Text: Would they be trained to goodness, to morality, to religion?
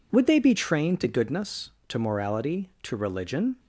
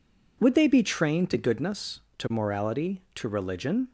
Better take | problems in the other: neither | none

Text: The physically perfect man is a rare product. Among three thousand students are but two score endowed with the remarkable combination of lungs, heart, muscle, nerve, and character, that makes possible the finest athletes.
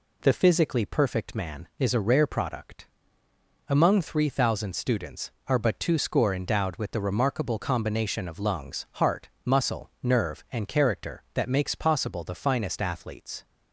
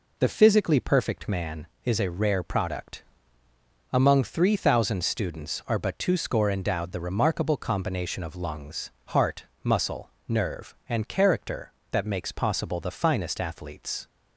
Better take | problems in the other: first | skips "with"; at 6.9 s

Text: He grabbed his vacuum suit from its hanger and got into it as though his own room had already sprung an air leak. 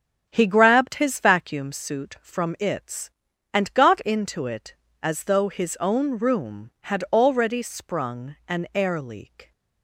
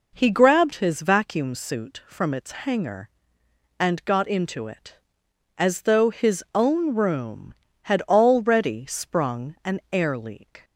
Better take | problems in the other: second | starts louder than the rest; until 1.3 s; 7 dB // skips "hanger"; at 3.3 s

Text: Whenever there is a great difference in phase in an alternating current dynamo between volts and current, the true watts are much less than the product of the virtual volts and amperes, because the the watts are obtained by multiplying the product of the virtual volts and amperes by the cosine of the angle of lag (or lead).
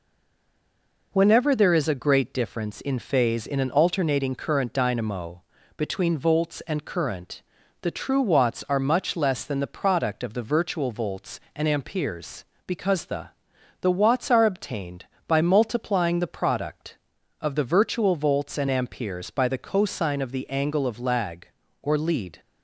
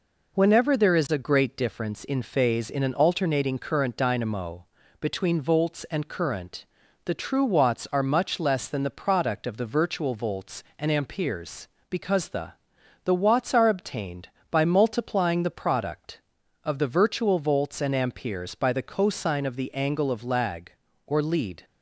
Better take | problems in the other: second | stays silent before the first word; until 1.1 s; 1.1 s long // pauses between "dynamo" and "between"; slight; at 5.4 s; 0.34 s long; slight in the second // pauses between "the" and "the"; noticeable; at 13.2 s; 0.52 s long; noticeable in the second

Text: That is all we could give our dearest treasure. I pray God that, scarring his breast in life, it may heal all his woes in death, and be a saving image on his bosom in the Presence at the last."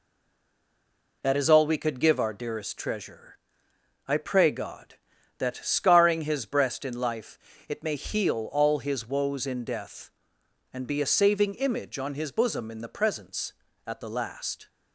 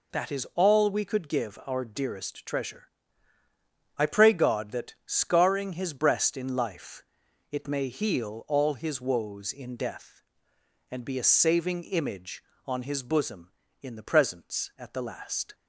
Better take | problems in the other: second | stays silent before the first word; noticeable; until 1.2 s; 1.2 s long

